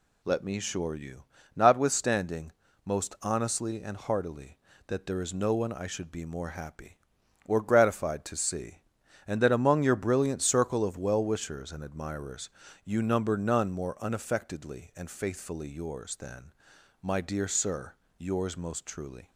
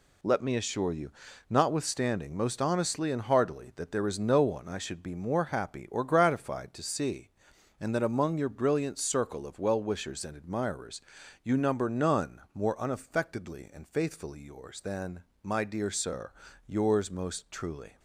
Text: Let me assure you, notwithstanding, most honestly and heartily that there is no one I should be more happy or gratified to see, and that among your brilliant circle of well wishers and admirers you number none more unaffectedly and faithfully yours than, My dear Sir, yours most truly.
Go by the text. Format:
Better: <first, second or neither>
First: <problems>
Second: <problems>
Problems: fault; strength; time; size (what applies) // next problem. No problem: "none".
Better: neither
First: pauses between "admirers" and "you"; slight; at 12.4 s; 0.36 s long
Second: pauses between "admirers" and "you"; at 11.0 s; 0.42 s long